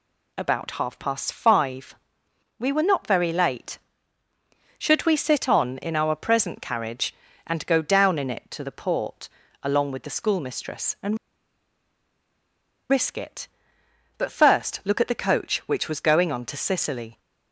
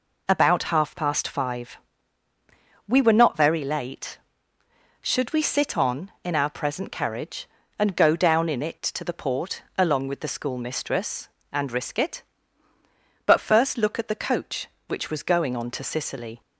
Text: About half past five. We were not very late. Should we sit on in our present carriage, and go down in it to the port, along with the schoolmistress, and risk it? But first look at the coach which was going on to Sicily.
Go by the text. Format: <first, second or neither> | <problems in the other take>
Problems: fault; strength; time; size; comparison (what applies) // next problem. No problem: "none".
second | pauses between "and" and "risk"; strong; at 11.1 s; 1.7 s long